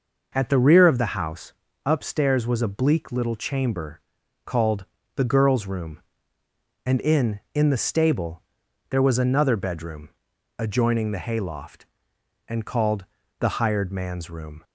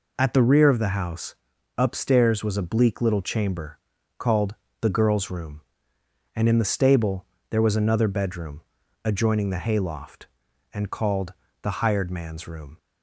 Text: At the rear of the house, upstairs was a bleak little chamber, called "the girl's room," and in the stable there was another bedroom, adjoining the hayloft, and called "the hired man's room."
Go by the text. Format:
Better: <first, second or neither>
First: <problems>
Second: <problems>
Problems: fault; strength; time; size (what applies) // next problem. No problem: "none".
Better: second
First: pauses between "called" and "the"; slight; at 4.8 s; 0.28 s long // says "in" twice; at 7.5 s // pauses between "stable" and "there"; noticeable; at 8.4 s; 0.48 s long // pauses between "called" and "the"; slight; at 13.0 s; 0.36 s long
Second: pauses between "called" and "the"; slight; at 4.5 s; 0.24 s long // pauses between "stable" and "there"; slight; at 7.2 s; 0.24 s long // pauses between "called" and "the"; slight; at 11.3 s; 0.30 s long